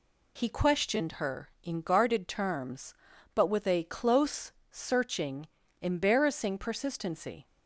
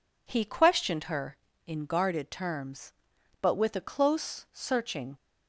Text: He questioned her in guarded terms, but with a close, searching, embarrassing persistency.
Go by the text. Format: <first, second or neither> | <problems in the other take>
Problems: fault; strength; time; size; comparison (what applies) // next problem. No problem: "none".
first | stops before "embarrassing persistency"; at 5.1 s